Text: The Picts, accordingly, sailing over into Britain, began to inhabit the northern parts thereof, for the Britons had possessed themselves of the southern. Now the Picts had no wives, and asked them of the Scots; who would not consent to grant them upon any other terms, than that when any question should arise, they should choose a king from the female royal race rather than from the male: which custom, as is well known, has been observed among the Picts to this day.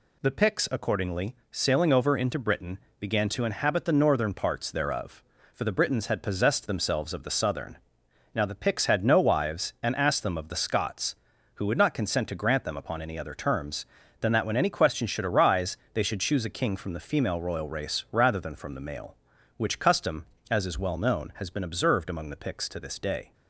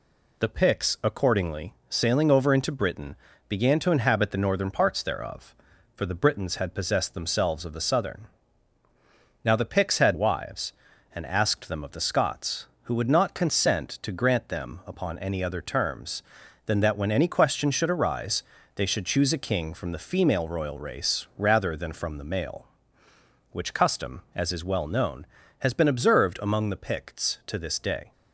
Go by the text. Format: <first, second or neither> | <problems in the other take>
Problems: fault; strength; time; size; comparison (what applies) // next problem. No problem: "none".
first | skips "no"; at 10.1 s